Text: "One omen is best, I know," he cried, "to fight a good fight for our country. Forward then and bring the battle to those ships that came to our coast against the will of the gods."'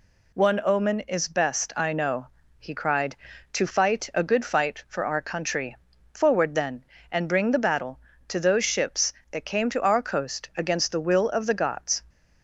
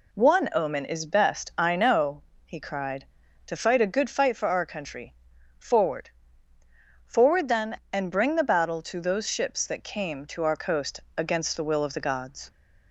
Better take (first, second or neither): first